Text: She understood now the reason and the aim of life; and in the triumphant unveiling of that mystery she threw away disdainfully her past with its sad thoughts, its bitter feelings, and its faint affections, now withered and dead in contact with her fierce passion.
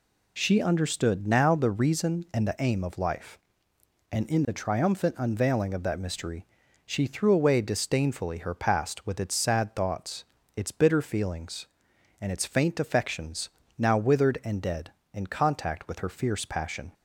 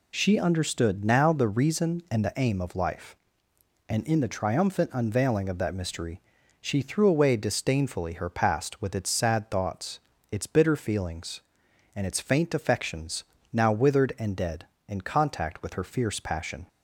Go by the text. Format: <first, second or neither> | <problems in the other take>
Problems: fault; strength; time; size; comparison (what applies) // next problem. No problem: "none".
neither | pauses between "mystery" and "she"; the same in both